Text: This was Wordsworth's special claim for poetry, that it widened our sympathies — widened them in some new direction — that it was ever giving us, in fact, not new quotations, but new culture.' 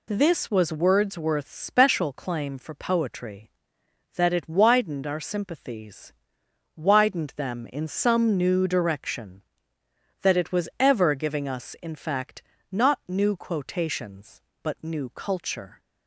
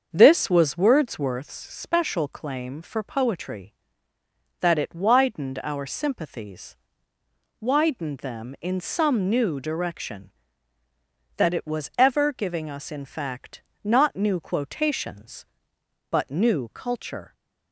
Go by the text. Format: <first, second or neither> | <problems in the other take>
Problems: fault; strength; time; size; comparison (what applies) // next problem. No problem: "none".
first | starts louder than the rest; until 1.3 s; 6.5 dB